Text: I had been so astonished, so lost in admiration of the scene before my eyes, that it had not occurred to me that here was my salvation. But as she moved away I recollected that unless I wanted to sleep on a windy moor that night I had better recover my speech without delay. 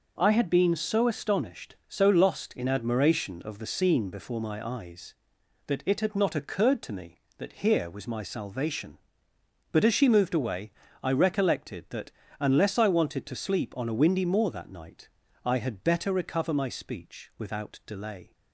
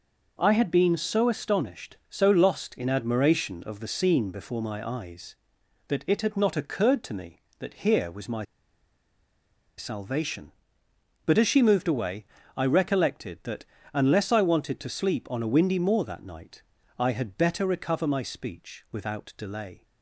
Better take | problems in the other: first | pauses between "my" and "salvation"; strong; at 8.4 s; 1.3 s long // pauses between "away" and "I"; slight; at 12.2 s; 0.32 s long; slight in the first // pauses between "that" and "unless"; slight; at 13.6 s; 0.28 s long; slight in the first // pauses between "night" and "I"; slight; at 16.6 s; 0.34 s long; slight in the first

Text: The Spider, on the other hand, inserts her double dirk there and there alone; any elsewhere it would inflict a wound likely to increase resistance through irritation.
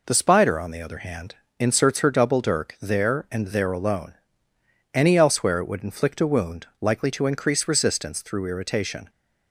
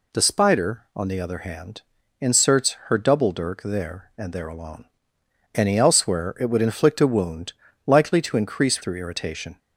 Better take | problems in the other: first | pauses between "wound" and "likely"; slight; at 7.5 s; 0.32 s long // skips "resistance"; at 8.8 s

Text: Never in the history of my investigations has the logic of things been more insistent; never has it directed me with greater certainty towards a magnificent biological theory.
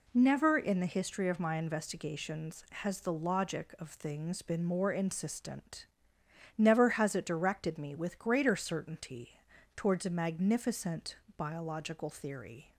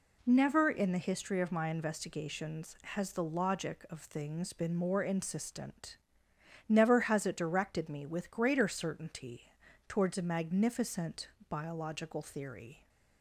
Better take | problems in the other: neither | pauses between "certainty" and "towards"; slight; the same in both // pauses between "magnificent" and "biological"; slight; the same in both

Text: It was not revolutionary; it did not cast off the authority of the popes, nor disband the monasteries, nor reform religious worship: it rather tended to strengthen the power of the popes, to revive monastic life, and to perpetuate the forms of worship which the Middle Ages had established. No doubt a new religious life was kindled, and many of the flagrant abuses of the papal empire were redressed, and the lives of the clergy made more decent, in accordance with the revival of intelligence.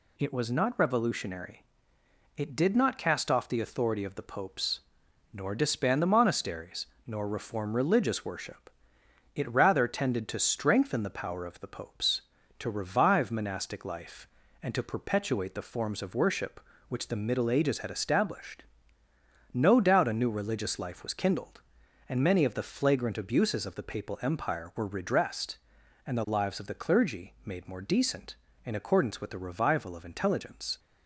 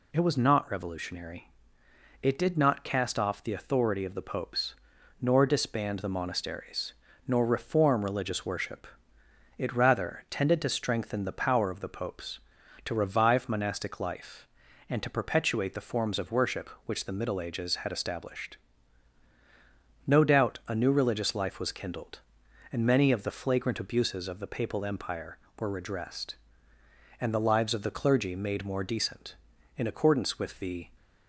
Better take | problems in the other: first | stops before "revival of intelligence"; at 30.9 s

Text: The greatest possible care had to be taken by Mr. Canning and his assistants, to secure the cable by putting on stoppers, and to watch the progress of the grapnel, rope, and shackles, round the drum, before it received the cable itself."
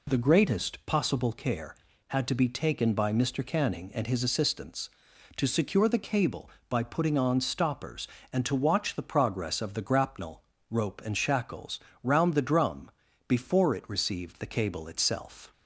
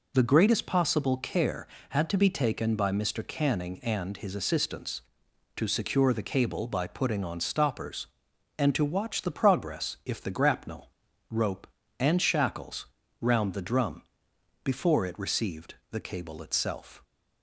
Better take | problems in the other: first | says "if" for "of"; at 10.0 s // pauses between "received" and "the"; slight; at 15.7 s; 0.16 s long

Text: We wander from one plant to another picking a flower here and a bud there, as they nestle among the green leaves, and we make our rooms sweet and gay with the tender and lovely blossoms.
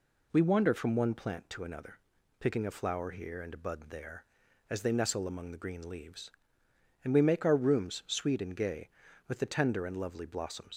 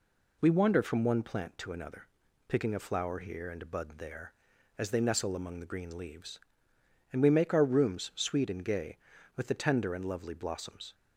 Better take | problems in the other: second | pauses between "another" and "picking"; at 1.9 s; 0.40 s long; also in the second // leaves "blossoms" unfinished; at 10.7 s; 95 ms

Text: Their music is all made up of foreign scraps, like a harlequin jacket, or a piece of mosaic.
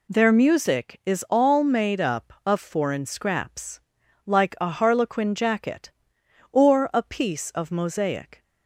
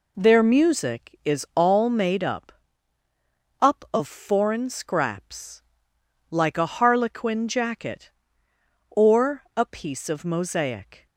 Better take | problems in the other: first | says "up" twice; at 3.5 s

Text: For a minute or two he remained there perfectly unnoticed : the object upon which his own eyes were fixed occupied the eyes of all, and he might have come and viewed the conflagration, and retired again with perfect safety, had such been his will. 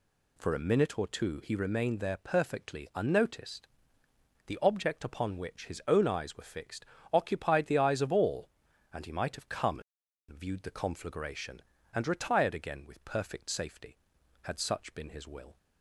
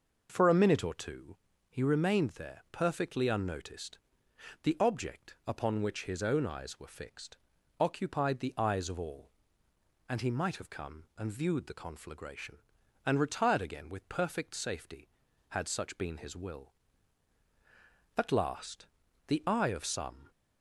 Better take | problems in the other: first | pauses between "two" and "he"; slight; at 1.3 s; 0.34 s long // pauses between "fixed" and "occupied"; at 7.3 s; 0.44 s long; slight in the first // goes on to say "At last the eye of some"; strong; from 18.1 s on; 2.1 s long

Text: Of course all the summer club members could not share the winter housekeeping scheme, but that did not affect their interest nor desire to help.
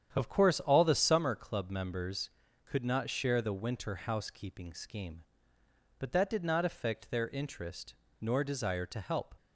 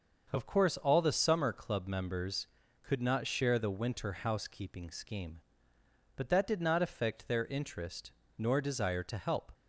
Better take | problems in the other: second | starts louder than the rest; strong; until 1.3 s; 9 dB // pauses between "interest" and "nor"; slight; at 7.9 s; 0.26 s long; slight in the second

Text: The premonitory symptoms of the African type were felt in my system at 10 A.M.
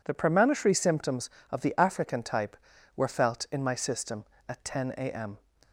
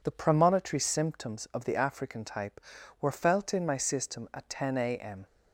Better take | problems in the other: neither | none

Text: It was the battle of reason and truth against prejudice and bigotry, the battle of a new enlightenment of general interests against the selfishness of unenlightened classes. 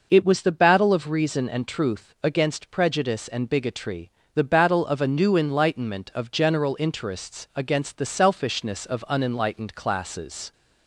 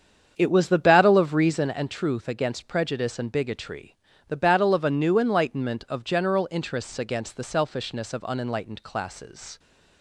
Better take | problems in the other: first | starts louder than the rest; strong; until 1.7 s; 7.5 dB

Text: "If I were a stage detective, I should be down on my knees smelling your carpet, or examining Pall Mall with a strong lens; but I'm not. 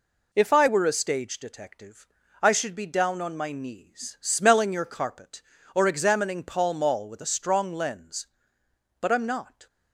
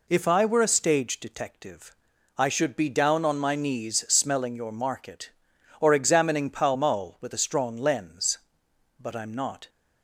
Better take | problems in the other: first | says "market" for "carpet"; at 4.7 s

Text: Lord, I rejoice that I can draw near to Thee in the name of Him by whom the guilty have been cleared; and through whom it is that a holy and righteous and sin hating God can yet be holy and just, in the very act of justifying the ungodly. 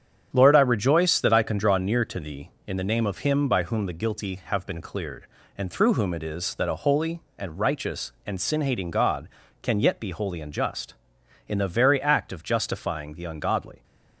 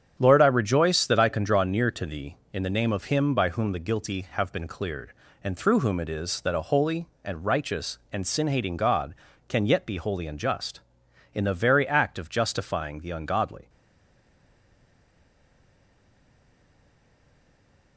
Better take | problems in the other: first | starts louder than the rest; strong; until 1.1 s; 8 dB; strong in the first // stays silent after the last word; strong; from 13.6 s on; 4.3 s long

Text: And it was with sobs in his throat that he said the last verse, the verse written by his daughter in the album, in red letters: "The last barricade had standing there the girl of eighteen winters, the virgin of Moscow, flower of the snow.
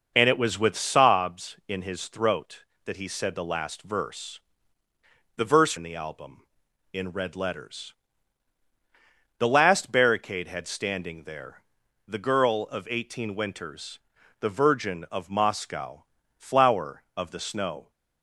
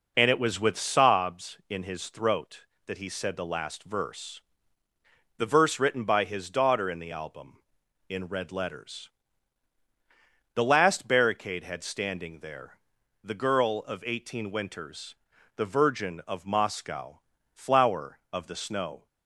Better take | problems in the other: second | skips "written by his daughter"; at 5.7 s // pauses between "there" and "the"; noticeable; at 11.6 s; 0.46 s long; noticeable in the second

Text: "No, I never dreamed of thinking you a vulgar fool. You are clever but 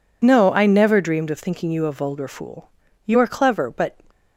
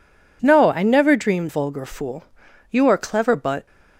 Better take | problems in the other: first | skips "of thinking you a"; at 1.4 s

